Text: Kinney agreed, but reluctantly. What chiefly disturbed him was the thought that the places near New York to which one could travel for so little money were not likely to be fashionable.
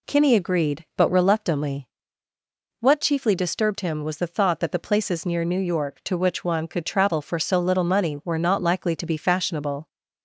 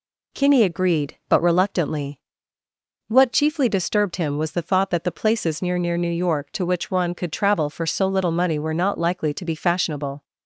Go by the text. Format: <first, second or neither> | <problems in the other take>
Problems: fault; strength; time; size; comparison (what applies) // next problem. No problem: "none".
first | says "near" twice; at 5.7 s